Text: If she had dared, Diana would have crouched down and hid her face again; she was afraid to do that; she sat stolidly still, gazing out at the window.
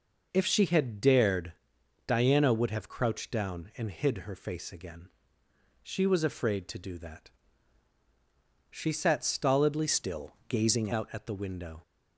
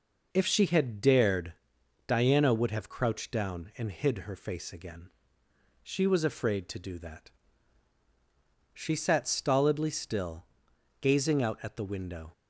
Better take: second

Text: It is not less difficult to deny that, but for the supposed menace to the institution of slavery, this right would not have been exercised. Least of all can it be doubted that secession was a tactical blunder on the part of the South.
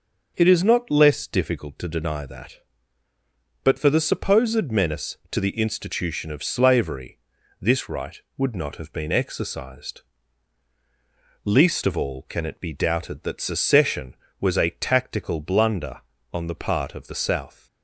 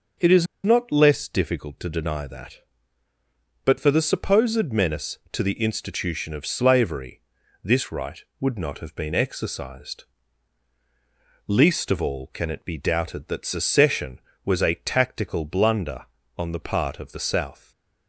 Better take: first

